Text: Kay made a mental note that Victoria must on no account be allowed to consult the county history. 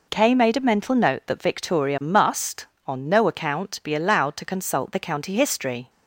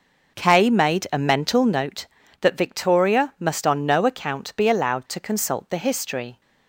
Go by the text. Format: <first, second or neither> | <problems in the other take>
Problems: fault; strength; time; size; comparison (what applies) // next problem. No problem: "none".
first | skips "county"; at 5.7 s